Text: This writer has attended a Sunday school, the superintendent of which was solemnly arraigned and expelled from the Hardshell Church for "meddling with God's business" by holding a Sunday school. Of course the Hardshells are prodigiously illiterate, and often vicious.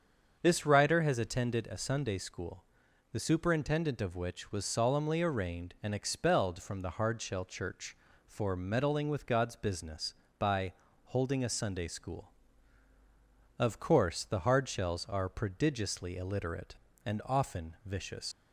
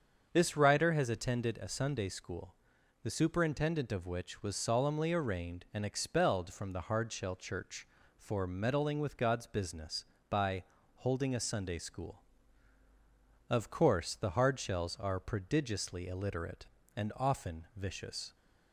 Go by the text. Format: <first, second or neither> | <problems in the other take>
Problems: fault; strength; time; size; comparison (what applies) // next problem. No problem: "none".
second | starts louder than the rest; strong; until 1.4 s; 7 dB; also in the second // pauses between "by" and "holding"; slight; at 10.7 s; 0.32 s long; slight in the second // leaves "vicious" unfinished; at 18.3 s; 125 ms